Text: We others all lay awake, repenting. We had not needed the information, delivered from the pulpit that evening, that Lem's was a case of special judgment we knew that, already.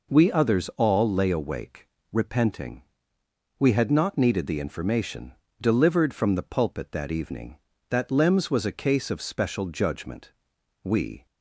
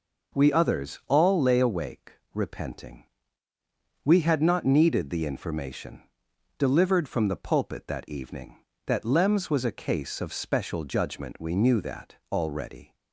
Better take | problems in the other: second | pauses between "judgment" and "we"; noticeable; at 10.3 s; 0.50 s long // stops before "knew that already"; at 11.2 s

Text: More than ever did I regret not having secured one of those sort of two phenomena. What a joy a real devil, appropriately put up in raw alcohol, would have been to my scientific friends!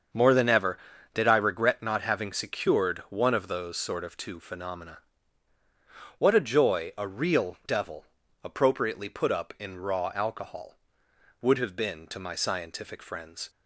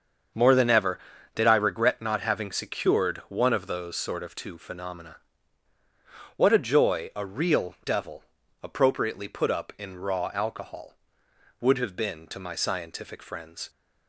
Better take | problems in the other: neither | starts louder than the rest; the same in both

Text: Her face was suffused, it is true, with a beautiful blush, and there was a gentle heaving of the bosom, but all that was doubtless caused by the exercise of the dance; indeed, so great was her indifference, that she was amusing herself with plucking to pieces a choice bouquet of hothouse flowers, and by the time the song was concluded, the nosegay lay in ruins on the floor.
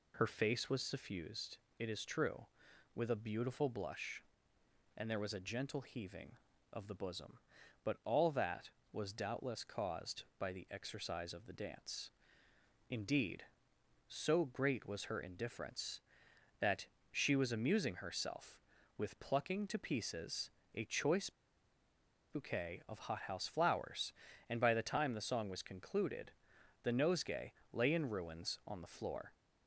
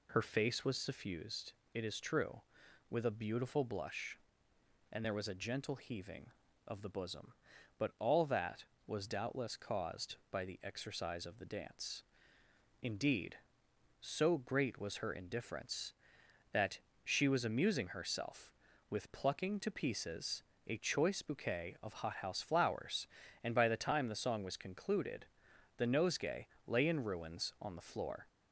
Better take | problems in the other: second | pauses between "that" and "she"; slight; at 16.8 s; 0.26 s long; slight in the second // pauses between "pieces" and "a"; slight; at 20.4 s; 0.24 s long; slight in the second // pauses between "choice" and "bouquet"; at 21.2 s; 1.0 s long // pauses between "nosegay" and "lay"; slight; at 27.5 s; 0.20 s long; slight in the second

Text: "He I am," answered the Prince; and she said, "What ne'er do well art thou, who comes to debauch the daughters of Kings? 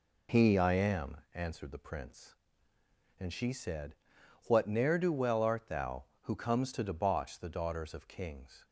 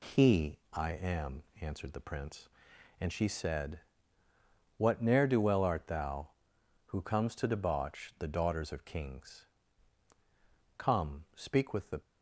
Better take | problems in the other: first | pauses between "He" and "I"; slight; at 0.5 s; 0.16 s long // goes on to say "Come speak with the"; noticeable; from 10.7 s on; 1.2 s long

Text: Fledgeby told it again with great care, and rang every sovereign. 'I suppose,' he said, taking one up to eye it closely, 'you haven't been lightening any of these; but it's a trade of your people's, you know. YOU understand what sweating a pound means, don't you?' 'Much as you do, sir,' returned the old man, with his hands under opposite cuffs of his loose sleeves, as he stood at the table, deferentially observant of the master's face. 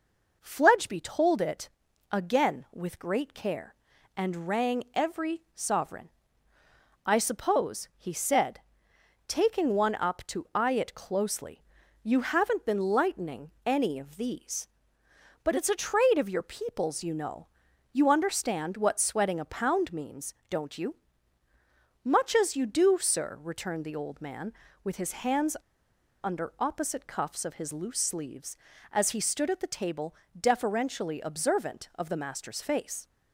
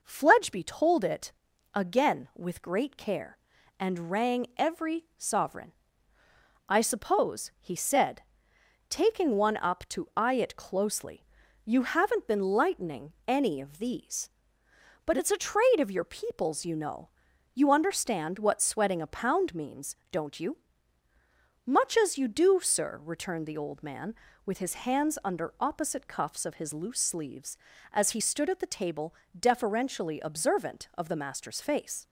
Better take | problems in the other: second | pauses between "it" and "again"; at 1.6 s; 0.42 s long; also in the second // pauses between "hands" and "under"; noticeable; at 25.5 s; 0.66 s long

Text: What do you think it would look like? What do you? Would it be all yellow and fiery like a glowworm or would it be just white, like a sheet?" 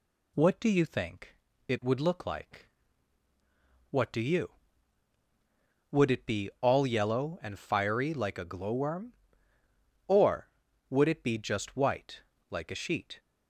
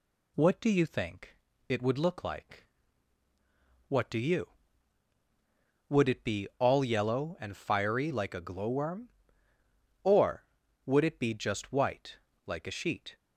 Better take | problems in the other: neither | pauses between "think" and "it"; slight; the same in both

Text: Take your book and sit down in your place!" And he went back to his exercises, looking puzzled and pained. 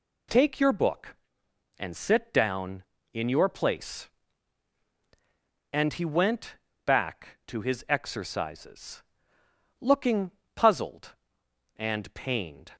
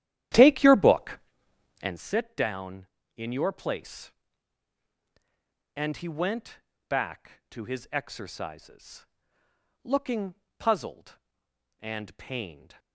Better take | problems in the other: first | starts louder than the rest; strong; until 2.0 s; 12 dB // pauses between "went" and "back"; slight; at 6.6 s; 0.28 s long; slight in the first // pauses between "looking" and "puzzled"; slight; at 10.3 s; 0.24 s long; slight in the first

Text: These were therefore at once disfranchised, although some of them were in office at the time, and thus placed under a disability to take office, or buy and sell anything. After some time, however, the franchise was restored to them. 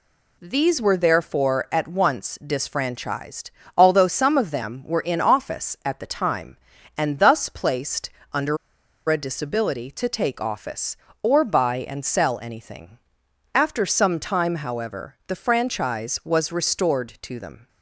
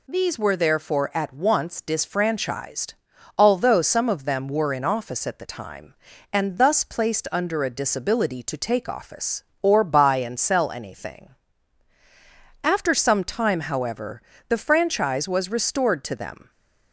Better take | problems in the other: second | pauses between "placed" and "under"; slight; at 8.1 s; 0.22 s long // pauses between "under" and "a"; noticeable; at 8.5 s; 0.52 s long

